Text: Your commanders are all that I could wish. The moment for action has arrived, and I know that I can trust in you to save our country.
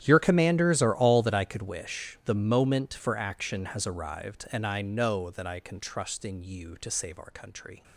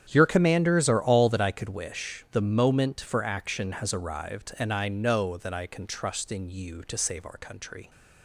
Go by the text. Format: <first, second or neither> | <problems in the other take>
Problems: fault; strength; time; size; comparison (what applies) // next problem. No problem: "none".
second | gets quieter; strong; throughout; 18.5 dB // starts louder than the rest; strong; until 1.0 s; 10.5 dB; strong in the second